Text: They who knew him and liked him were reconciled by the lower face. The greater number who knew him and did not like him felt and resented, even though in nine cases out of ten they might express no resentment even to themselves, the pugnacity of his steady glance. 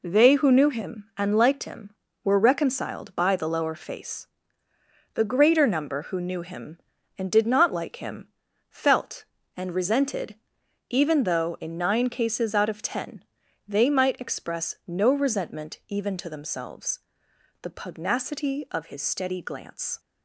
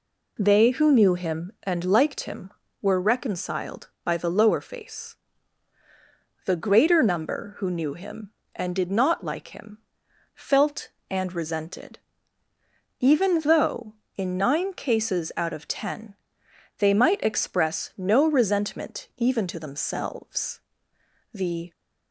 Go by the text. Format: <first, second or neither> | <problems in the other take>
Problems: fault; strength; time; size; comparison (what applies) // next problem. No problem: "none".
first | pauses between "him" and "felt"; noticeable; at 9.7 s; 0.58 s long; also in the first // pauses between "ten" and "they"; noticeable; at 16.1 s; 0.64 s long; also in the first // stops before "pugnacity of his steady glance"; at 21.7 s